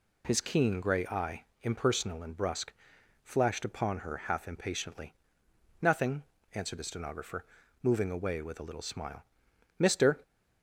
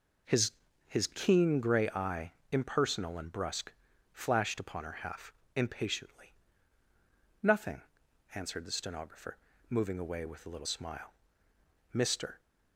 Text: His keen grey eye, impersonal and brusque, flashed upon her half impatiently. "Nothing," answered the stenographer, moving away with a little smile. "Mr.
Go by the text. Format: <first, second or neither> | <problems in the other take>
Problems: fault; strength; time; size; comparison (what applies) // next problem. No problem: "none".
first | says "His" twice; at 0.8 s // pauses between "half" and "impatiently"; slight; at 5.3 s; 0.22 s long